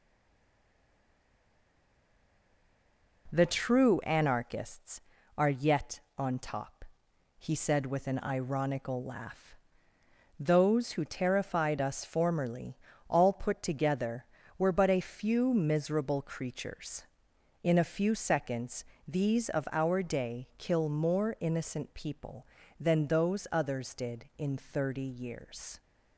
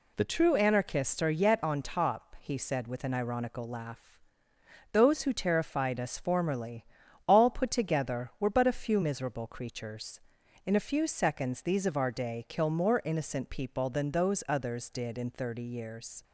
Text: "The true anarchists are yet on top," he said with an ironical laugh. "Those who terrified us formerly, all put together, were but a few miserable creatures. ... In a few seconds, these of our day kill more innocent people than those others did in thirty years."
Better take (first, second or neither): second